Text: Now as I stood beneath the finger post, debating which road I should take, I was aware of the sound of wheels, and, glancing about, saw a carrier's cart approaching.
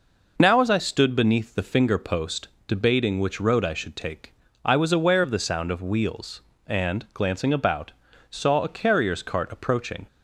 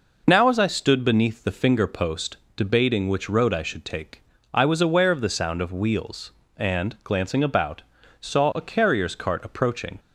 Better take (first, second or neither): neither